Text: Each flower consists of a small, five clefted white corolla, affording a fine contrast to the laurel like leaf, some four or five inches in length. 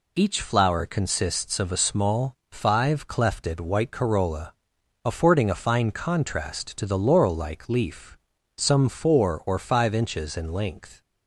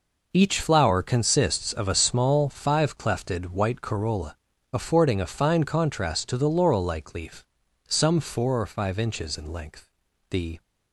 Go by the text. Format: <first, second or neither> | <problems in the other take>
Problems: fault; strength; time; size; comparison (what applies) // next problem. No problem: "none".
first | goes on to say "The"; slight; from 10.2 s on; 0.32 s long